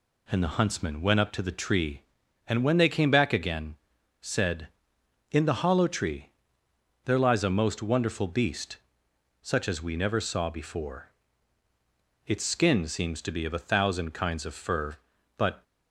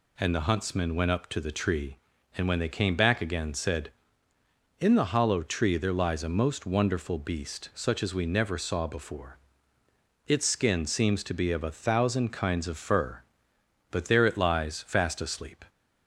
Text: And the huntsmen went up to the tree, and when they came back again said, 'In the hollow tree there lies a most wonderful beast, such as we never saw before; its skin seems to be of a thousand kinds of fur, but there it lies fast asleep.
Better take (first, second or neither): second